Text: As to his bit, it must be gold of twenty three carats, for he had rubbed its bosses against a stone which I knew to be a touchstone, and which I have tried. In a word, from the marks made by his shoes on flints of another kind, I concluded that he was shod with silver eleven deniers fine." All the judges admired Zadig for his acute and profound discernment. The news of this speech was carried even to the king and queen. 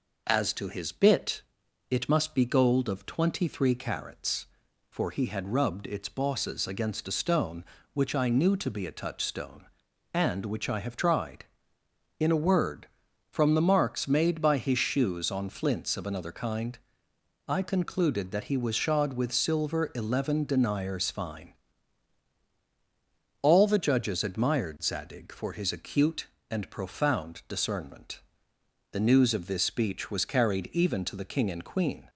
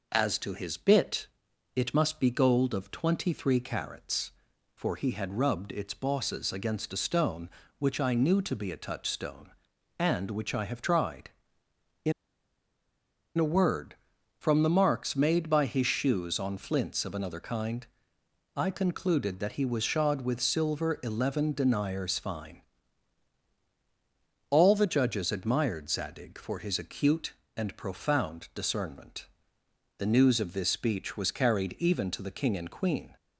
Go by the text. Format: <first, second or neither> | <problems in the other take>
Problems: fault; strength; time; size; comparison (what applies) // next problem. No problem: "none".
first | pauses between "In" and "a"; strong; at 12.1 s; 1.2 s long